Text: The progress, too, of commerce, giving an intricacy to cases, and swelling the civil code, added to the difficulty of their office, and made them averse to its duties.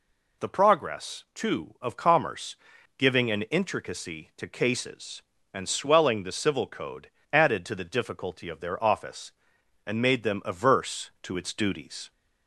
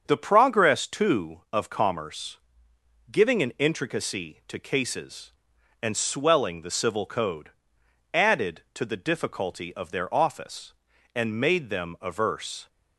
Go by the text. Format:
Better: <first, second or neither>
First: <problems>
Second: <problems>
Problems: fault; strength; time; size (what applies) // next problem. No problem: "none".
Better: first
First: none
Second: starts louder than the rest; until 1.0 s; 6.5 dB // stops before "to its duties"; at 12.6 s